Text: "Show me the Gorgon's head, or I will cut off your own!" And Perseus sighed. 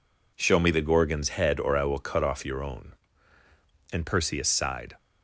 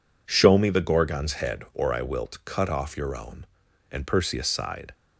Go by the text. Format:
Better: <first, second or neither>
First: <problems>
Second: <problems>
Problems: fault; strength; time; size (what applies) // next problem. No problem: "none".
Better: first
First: none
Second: says "wilt" for "will"; at 2.0 s